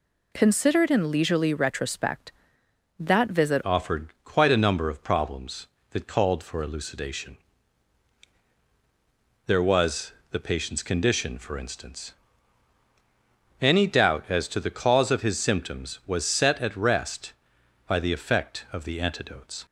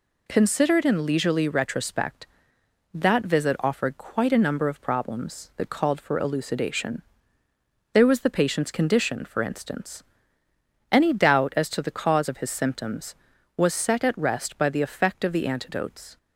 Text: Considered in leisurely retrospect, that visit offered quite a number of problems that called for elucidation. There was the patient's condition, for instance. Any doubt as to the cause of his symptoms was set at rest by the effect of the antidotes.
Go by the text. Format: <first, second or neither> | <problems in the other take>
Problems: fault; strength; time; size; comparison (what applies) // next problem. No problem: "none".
second | changes voice at "offered"; from 3.6 s on; 16.0 s long // pauses between "offered" and "quite"; slight; at 4.0 s; 0.16 s long // pauses between "was" and "the"; slight; at 10.1 s; 0.20 s long